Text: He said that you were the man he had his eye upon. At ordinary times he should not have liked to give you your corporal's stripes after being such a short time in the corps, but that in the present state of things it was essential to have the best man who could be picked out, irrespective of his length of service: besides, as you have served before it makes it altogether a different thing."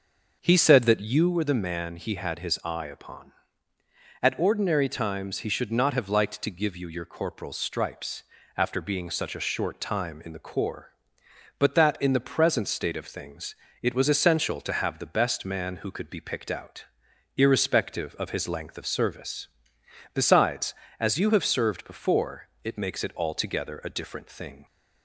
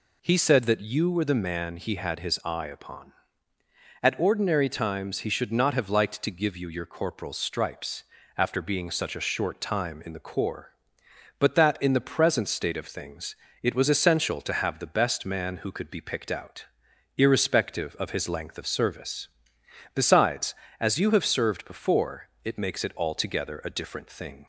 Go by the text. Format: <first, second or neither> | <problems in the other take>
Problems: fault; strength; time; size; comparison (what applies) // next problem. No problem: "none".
second | starts louder than the rest; until 1.3 s; 6 dB // pauses between "stripes" and "after"; slight; at 8.2 s; 0.32 s long; slight in the second // pauses between "things" and "it"; slight; at 13.5 s; 0.26 s long; slight in the second // pauses between "before" and "it"; slight; at 22.4 s; 0.16 s long; slight in the second